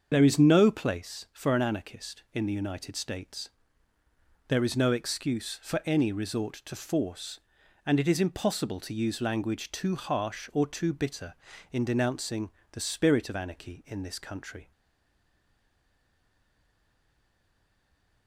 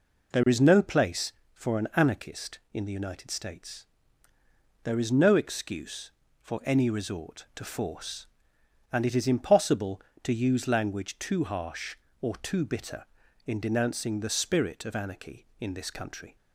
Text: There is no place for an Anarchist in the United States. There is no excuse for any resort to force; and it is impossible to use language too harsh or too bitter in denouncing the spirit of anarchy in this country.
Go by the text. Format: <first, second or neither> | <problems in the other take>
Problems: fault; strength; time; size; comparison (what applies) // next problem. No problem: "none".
second | starts louder than the rest; until 1.1 s; 7 dB // pauses between "denouncing" and "the"; slight; at 12.5 s; 0.22 s long // stays silent after the last word; strong; from 14.7 s on; 3.5 s long